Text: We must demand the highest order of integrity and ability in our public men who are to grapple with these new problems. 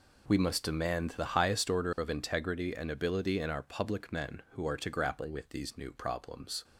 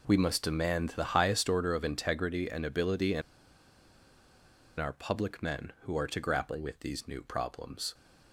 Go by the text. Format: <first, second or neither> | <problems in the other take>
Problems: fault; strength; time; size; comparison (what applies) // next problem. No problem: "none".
first | pauses between "in" and "our"; strong; at 3.2 s; 1.5 s long